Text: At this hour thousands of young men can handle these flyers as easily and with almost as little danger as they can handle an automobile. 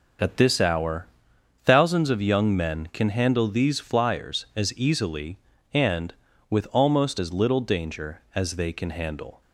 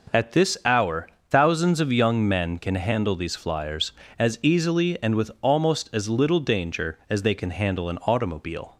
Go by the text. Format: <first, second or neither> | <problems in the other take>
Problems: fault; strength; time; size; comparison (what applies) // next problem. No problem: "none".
second | pauses between "hour" and "thousands"; noticeable; at 1.0 s; 0.58 s long; slight in the second // stops before "an automobile"; at 9.4 s